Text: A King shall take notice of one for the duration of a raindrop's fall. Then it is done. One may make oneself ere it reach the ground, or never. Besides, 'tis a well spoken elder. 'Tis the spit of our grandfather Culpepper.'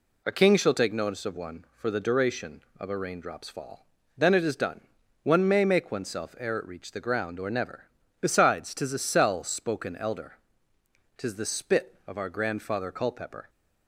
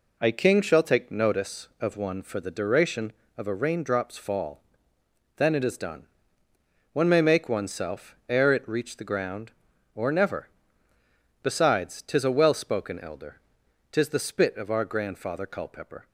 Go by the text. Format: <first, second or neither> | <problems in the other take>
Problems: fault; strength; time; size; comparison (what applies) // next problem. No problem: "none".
second | says "cell" for "well"; at 8.9 s